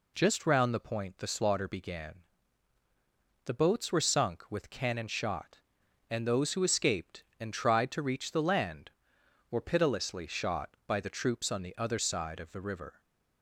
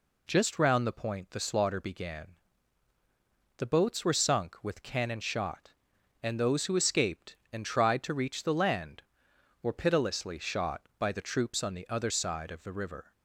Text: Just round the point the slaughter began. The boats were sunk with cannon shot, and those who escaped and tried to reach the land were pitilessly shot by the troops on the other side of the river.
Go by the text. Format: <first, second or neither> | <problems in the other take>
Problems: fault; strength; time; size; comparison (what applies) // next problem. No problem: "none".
neither | none